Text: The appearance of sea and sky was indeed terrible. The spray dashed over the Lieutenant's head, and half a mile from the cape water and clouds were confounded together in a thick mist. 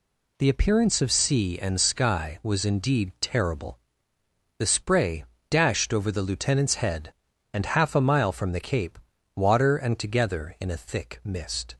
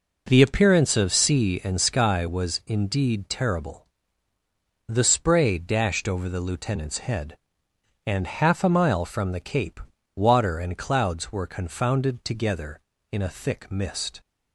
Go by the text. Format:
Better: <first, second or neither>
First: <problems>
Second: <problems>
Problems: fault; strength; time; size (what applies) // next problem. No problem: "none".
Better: second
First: pauses between "spray" and "dashed"; slight; at 5.2 s; 0.26 s long // pauses between "cape" and "water"; at 8.9 s; 0.38 s long // skips "clouds were confounded"; at 9.9 s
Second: pauses between "cape" and "water"; slight; at 9.7 s; 0.36 s long